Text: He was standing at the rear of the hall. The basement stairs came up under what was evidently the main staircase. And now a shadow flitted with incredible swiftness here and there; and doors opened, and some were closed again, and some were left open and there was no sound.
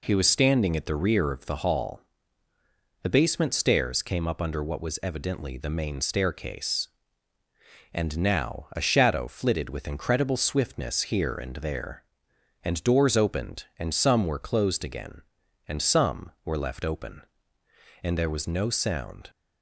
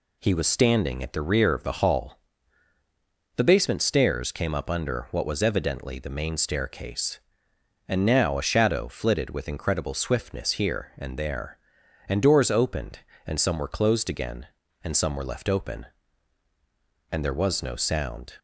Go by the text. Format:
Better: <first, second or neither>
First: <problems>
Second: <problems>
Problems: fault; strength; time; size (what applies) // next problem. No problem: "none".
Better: neither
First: none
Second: none